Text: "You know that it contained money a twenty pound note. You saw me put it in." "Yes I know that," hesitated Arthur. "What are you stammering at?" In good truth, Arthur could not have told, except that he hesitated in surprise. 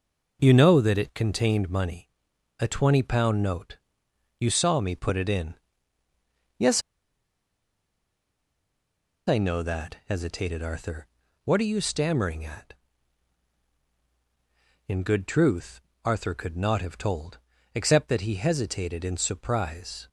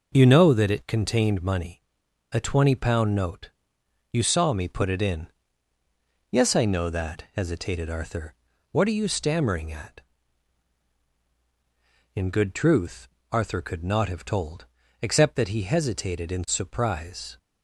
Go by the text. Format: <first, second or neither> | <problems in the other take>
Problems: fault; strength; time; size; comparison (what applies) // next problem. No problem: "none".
second | pauses between "money" and "a"; noticeable; at 2.0 s; 0.50 s long; noticeable in the second // pauses between "Yes" and "I"; strong; at 6.8 s; 2.4 s long